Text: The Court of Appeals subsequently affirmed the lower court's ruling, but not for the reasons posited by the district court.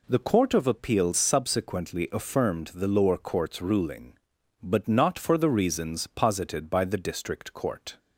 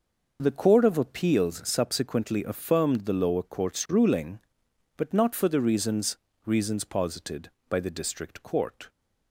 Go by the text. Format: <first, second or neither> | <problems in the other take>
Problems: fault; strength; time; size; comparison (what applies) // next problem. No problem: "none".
first | says "reasons" twice; at 6.4 s